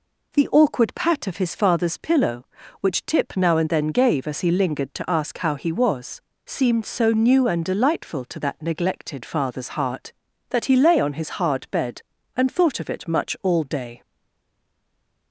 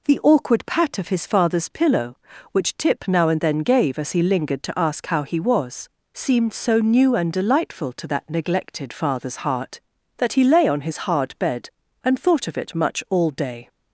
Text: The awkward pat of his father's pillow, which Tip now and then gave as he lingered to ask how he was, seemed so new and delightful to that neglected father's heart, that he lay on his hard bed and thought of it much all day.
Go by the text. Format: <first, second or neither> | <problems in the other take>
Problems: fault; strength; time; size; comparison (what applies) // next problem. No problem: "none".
second | stays silent after the last word; noticeable; from 14.0 s on; 1.3 s long